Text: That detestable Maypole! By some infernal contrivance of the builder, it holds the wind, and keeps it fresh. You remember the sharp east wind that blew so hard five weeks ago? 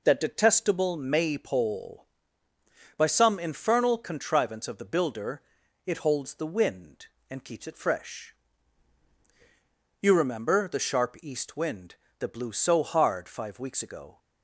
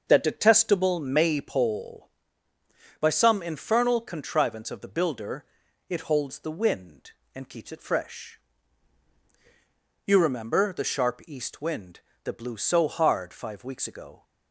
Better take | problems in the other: first | starts louder than the rest; until 1.7 s; 6.5 dB

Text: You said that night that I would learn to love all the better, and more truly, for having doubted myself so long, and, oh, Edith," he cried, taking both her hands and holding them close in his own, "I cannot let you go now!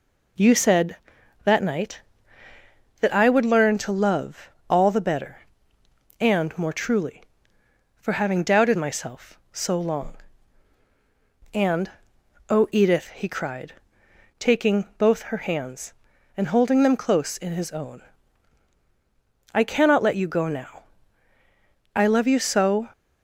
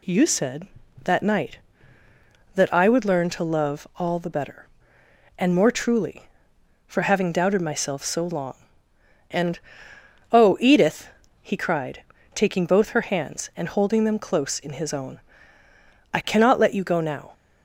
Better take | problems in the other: second | pauses between "love" and "all"; slight; at 4.5 s; 0.18 s long // goes on to say "I love you so"; noticeable; from 21.9 s on; 0.96 s long

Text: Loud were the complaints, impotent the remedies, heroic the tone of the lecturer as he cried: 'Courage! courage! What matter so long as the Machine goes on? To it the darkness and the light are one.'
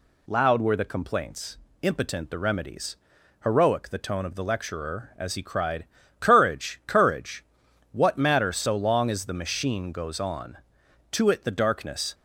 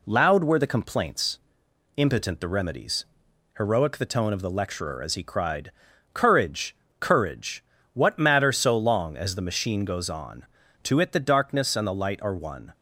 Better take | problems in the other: second | stops before "and the light are one"; at 12.1 s

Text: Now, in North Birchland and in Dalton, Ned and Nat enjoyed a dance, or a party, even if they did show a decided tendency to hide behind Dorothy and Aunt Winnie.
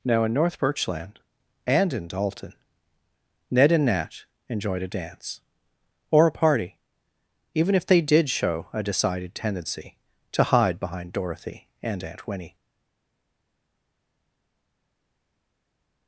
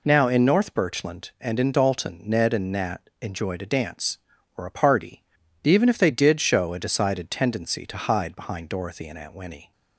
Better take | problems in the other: second | pauses between "Nat" and "enjoyed"; slight; at 4.2 s; 0.24 s long // stays silent after the last word; strong; from 12.5 s on; 3.5 s long

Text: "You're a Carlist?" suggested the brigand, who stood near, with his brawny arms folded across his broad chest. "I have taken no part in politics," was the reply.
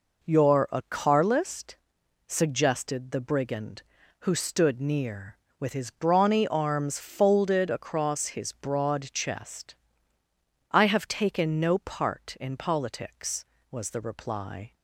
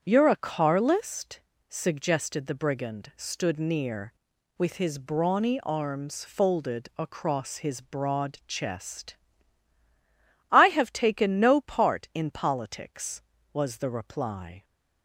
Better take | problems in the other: first | starts louder than the rest; strong; until 1.0 s; 8 dB // skips "who"; at 3.1 s

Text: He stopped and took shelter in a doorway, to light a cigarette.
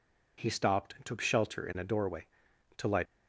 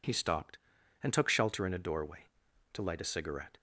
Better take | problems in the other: second | stops before "a cigarette"; at 3.0 s

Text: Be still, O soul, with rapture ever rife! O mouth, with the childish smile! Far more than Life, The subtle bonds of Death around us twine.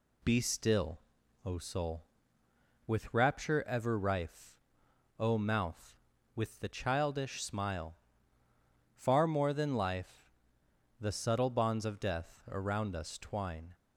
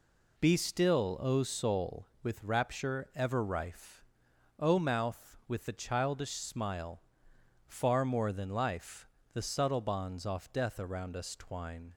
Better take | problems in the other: first | says "off" for "of"; at 10.2 s

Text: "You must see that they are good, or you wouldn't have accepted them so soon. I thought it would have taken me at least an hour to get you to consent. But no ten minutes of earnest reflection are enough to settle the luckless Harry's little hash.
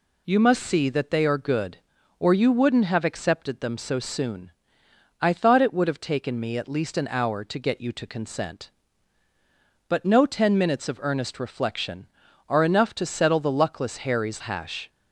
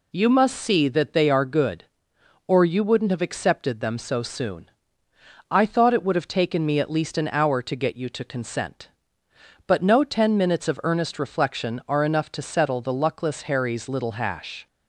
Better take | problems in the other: second | skips "little"; at 14.4 s

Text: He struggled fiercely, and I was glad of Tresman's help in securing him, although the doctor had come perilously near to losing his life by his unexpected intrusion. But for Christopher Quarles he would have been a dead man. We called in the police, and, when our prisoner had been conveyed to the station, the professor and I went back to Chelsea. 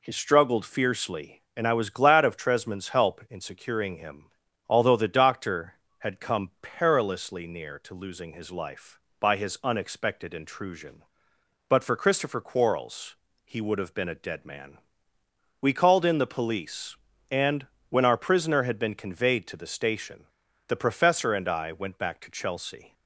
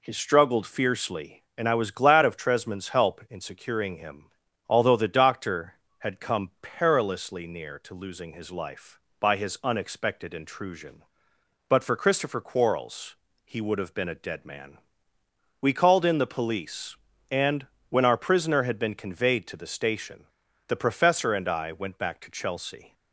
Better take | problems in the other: neither | pauses between "Quarles" and "he"; slight; the same in both

